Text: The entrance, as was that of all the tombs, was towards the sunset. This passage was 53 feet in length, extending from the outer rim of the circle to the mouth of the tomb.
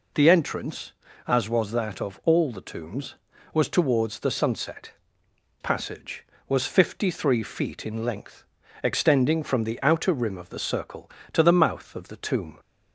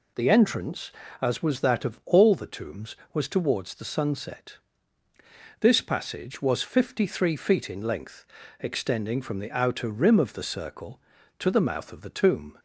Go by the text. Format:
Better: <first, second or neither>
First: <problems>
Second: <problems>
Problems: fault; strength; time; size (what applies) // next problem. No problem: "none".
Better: second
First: skips "This"; at 5.2 s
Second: none